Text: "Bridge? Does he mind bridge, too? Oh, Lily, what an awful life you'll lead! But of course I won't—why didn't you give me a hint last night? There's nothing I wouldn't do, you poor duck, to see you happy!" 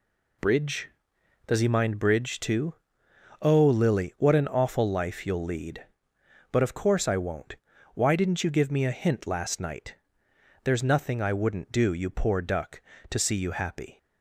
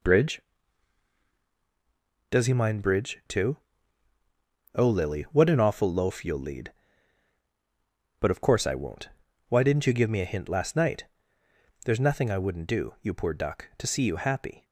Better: first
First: none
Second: says "loaf" for "life"; at 5.9 s

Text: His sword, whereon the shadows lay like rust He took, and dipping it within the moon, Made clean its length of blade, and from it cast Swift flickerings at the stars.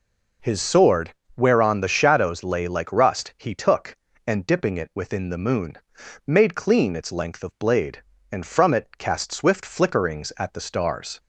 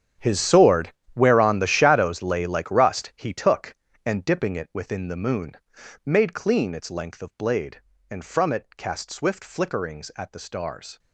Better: first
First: none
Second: gets quieter; strong; throughout; 16.5 dB

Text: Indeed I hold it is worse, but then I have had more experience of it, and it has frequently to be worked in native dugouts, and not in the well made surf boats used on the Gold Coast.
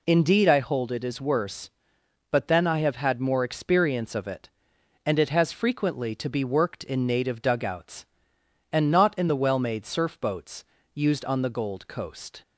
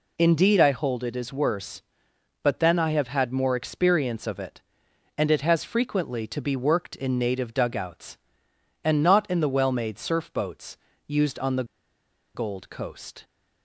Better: first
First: pauses between "boats" and "used"; slight; at 10.6 s; 0.28 s long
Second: pauses between "boats" and "used"; slight; at 10.7 s; 0.28 s long // pauses between "the" and "Gold"; noticeable; at 11.6 s; 0.70 s long

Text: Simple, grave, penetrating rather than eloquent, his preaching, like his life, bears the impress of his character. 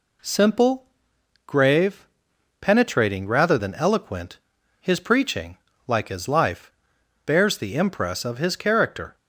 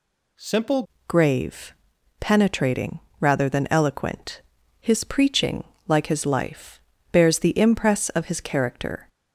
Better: first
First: none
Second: changes voice at "grave"; from 1.0 s on; 8.0 s long // pauses between "penetrating" and "rather"; slight; at 2.9 s; 0.20 s long

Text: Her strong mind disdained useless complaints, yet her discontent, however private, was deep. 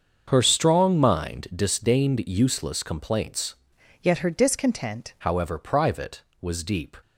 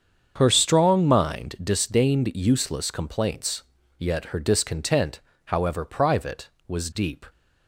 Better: second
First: starts louder than the rest; until 1.2 s; 6.5 dB // changes voice from "yet" to "discontent"; from 4.0 to 5.1 s; 1.1 s long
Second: starts louder than the rest; strong; until 1.3 s; 7 dB

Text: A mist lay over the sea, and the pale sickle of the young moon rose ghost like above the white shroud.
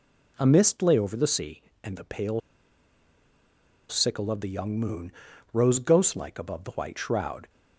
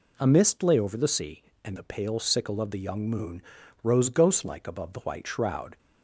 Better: second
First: pauses between "pale" and "sickle"; strong; at 2.4 s; 1.4 s long // pauses between "moon" and "rose"; at 5.1 s; 0.42 s long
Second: pauses between "moon" and "rose"; at 3.4 s; 0.42 s long

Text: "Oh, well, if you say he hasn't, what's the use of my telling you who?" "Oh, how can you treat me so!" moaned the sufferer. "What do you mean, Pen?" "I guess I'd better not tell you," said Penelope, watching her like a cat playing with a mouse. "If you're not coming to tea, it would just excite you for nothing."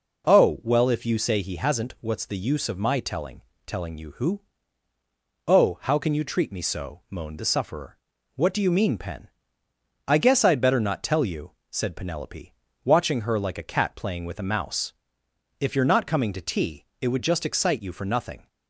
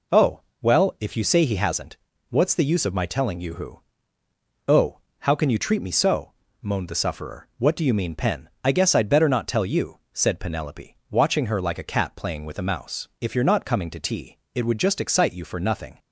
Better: second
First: says "telling" twice; at 3.6 s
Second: none

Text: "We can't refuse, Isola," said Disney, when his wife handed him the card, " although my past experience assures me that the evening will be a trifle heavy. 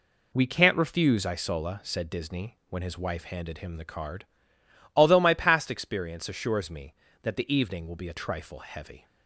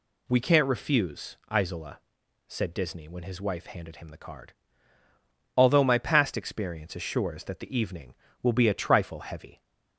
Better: first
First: none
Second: skips "me"; at 7.4 s

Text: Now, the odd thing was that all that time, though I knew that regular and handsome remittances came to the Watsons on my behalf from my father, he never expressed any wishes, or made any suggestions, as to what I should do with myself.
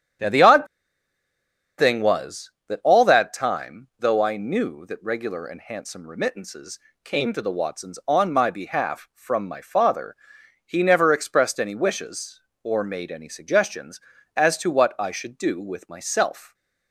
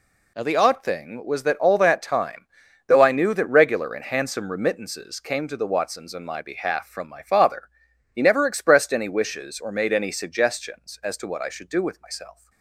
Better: second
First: starts louder than the rest; strong; until 2.3 s; 9 dB // pauses between "odd" and "thing"; at 0.6 s; 1.1 s long // pauses between "remittances" and "came"; slight; at 6.7 s; 0.28 s long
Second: none

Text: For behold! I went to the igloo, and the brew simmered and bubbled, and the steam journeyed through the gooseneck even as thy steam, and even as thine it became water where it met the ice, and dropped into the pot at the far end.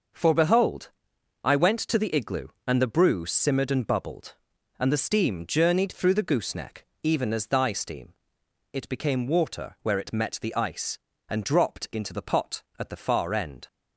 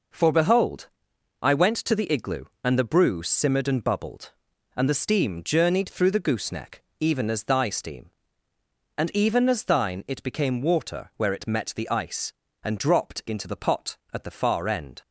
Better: second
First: starts louder than the rest; noticeable; until 1.6 s; 6 dB // pauses between "gooseneck" and "even"; slight; at 6.8 s; 0.16 s long // skips "and even as thine"; at 8.4 s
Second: pauses between "gooseneck" and "even"; slight; at 6.8 s; 0.16 s long

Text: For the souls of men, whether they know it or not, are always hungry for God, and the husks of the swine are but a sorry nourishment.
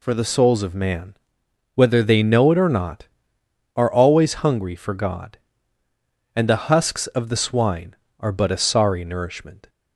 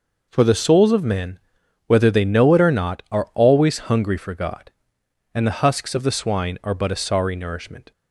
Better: second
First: says "man" for "men"; at 0.7 s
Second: none

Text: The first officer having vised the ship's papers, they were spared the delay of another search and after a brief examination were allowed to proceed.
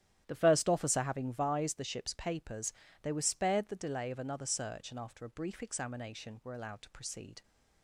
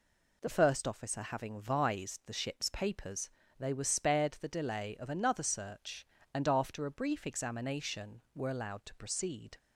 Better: second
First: starts louder than the rest; strong; until 1.7 s; 11.5 dB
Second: none

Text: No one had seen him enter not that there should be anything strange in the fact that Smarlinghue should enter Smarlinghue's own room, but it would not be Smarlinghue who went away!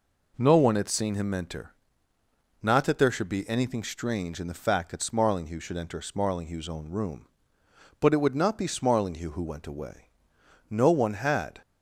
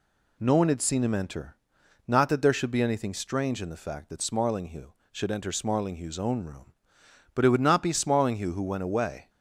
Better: second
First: pauses between "enter" and "not"; noticeable; at 1.7 s; 0.90 s long // goes on to say "No one had"; noticeable; from 10.7 s on; 0.90 s long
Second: pauses between "enter" and "not"; noticeable; at 1.5 s; 0.52 s long

